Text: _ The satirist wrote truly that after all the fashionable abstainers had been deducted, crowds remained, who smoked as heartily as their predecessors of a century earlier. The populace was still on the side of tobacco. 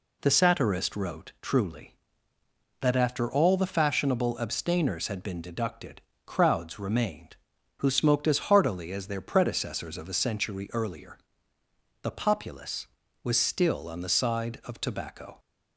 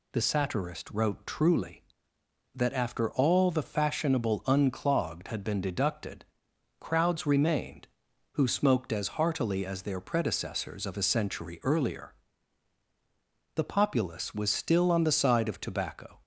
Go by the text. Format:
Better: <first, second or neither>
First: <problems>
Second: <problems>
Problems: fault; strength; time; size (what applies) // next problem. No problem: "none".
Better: first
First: none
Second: says "unclogged" for "abstainers"; at 4.4 s